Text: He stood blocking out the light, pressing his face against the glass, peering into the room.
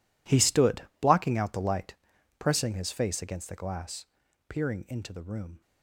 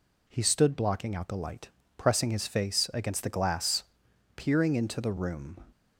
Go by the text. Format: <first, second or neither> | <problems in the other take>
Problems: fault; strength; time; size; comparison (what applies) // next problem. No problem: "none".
second | gets quieter; strong; throughout; 17 dB // pauses between "stood" and "blocking"; slight; at 0.8 s; 0.16 s long